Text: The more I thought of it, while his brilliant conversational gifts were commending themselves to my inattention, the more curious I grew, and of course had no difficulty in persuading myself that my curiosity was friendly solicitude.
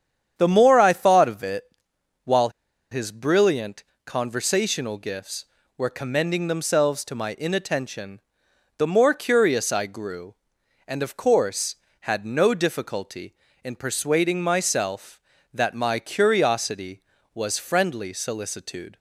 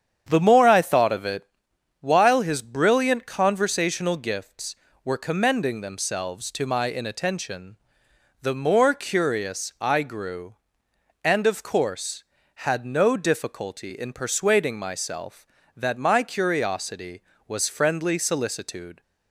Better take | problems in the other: second | starts louder than the rest; strong; until 1.3 s; 8.5 dB; strong in the second // pauses between "while" and "his"; at 2.5 s; 0.41 s long // pauses between "brilliant" and "conversational"; slight; at 3.8 s; 0.20 s long

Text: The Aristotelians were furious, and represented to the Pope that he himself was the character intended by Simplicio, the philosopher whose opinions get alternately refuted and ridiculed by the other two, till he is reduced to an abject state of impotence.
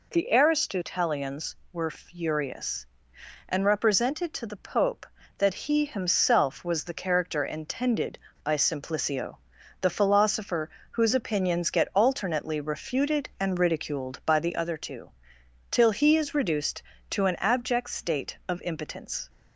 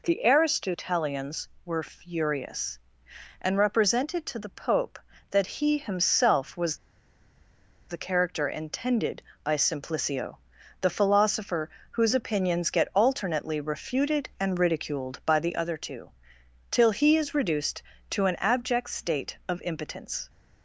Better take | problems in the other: first | pauses between "was" and "the"; at 6.7 s; 1.1 s long // pauses between "philosopher" and "whose"; slight; at 11.6 s; 0.22 s long; slight in the first

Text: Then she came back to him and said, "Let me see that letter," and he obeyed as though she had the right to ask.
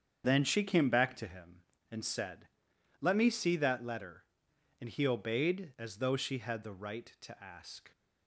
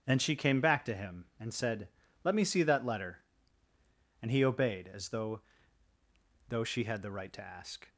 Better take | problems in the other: first | starts louder than the rest; strong; until 1.0 s; 7.5 dB; strong in the first // says "though" twice; at 6.4 s

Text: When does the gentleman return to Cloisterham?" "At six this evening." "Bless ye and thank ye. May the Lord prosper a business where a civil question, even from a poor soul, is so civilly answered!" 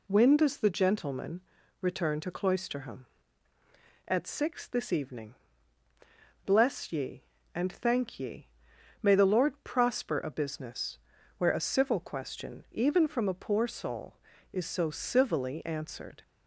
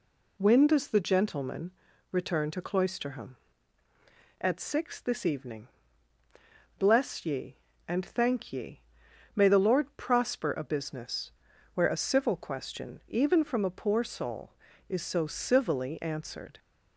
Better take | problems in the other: neither | pauses between "gentleman" and "return"; the same in both // pauses between "business" and "where"; the same in both

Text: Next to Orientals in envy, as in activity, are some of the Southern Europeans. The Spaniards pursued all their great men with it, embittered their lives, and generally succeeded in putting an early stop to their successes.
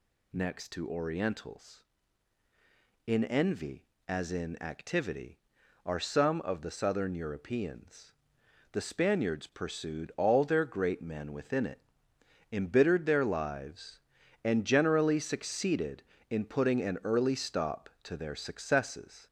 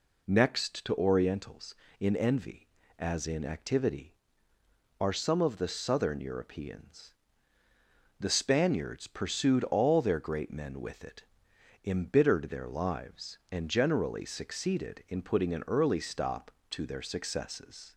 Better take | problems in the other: second | says "within" for "with"; at 11.3 s

